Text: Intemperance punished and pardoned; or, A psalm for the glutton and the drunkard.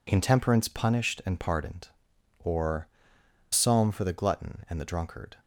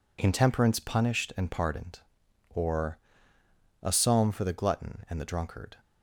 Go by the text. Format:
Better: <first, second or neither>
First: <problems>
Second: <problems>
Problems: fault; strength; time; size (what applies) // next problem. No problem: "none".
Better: second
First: skips "A"; at 3.2 s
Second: none